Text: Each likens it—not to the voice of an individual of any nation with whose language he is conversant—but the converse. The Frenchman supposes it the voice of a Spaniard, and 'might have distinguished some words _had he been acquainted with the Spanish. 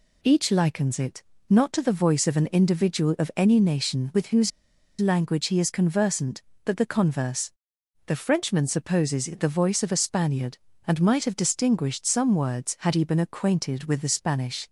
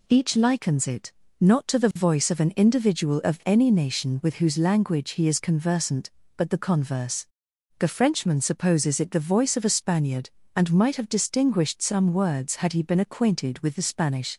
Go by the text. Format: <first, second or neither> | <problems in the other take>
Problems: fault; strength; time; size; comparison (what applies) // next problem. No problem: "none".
second | pauses between "whose" and "language"; noticeable; at 4.5 s; 0.49 s long